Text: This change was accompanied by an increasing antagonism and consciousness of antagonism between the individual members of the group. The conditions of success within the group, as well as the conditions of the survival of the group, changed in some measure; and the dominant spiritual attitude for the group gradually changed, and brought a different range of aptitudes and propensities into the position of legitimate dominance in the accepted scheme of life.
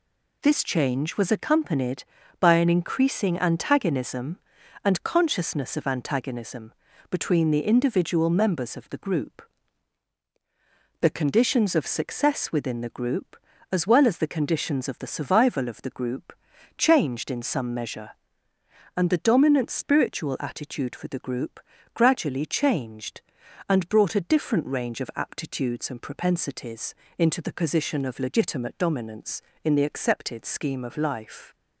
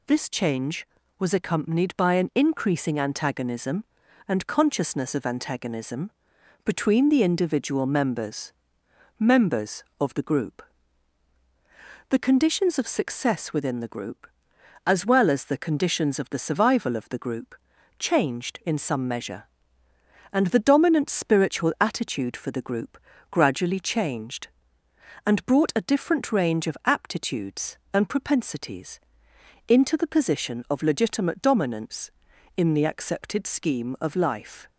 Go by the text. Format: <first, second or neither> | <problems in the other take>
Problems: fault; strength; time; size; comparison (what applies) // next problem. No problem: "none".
first | pauses between "antagonism" and "between"; noticeable; at 6.1 s; 0.54 s long; also in the first // says "members" twice; at 9.1 s // pauses between "group" and "gradually"; slight; at 22.9 s; 0.32 s long; slight in the first // pauses between "propensities" and "into"; noticeable; at 28.9 s; 0.68 s long; slight in the first